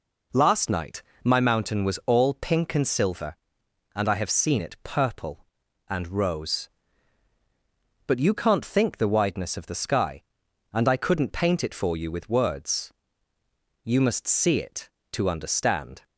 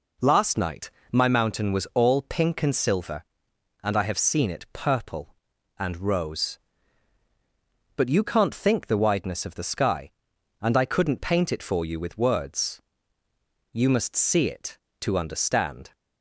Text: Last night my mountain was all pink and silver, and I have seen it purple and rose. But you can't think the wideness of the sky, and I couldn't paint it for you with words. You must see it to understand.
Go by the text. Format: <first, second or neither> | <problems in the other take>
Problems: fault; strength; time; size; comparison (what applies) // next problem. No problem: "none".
neither | pauses between "night" and "my"; slight; the same in both